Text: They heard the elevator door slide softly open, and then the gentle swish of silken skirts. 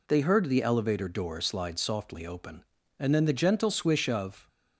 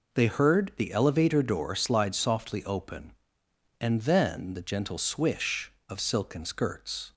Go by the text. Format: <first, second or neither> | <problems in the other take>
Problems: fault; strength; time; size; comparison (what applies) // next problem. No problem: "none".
second | stops before "silken skirts"; at 4.4 s